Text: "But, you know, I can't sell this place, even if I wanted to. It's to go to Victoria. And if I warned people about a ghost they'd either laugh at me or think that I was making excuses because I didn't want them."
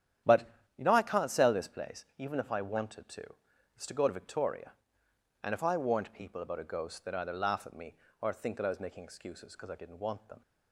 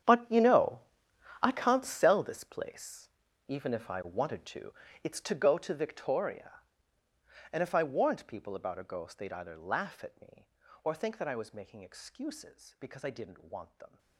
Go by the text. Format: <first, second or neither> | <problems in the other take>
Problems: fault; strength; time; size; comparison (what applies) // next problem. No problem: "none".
first | gets quieter; strong; throughout; 17.5 dB // starts louder than the rest; strong; until 1.7 s; 9 dB; strong in the first